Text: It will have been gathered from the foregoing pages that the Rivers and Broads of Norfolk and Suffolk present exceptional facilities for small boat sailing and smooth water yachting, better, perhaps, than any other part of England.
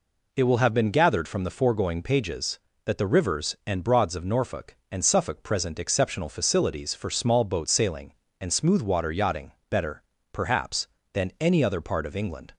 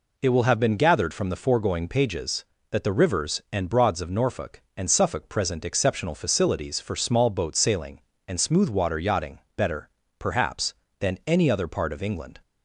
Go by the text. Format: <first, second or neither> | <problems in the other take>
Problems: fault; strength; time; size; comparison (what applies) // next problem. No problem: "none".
neither | none